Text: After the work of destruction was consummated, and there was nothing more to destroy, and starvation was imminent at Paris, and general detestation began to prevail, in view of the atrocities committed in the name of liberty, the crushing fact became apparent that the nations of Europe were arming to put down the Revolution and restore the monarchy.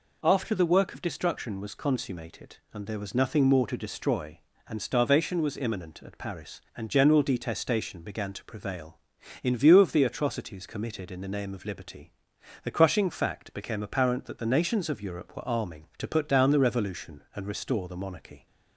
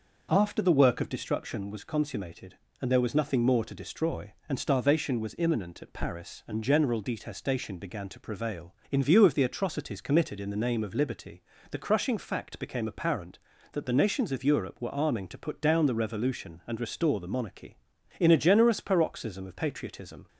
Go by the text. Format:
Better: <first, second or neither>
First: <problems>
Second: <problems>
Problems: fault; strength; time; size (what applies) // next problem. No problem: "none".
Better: first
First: none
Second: goes on to say "In a generous paroxysm of patriotism"; strong; from 18.1 s on; 2.0 s long